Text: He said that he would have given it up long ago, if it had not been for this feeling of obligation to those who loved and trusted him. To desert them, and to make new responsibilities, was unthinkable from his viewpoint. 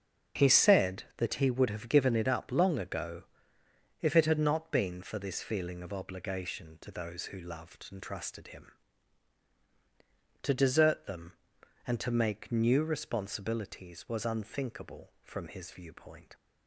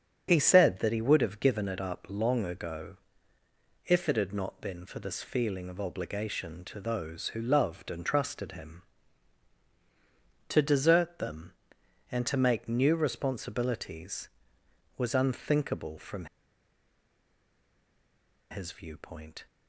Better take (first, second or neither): first